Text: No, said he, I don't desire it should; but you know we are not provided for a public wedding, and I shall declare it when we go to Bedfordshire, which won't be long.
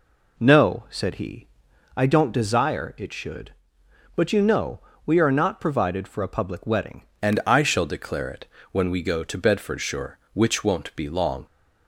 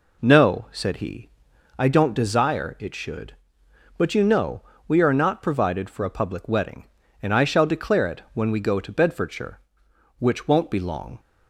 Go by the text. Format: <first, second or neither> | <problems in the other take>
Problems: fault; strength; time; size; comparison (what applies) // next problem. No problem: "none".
second | pauses between "know" and "we"; slight; at 4.8 s; 0.26 s long; slight in the second // changes voice at "and"; from 7.2 s on; 4.2 s long // pauses between "it" and "when"; slight; at 8.4 s; 0.26 s long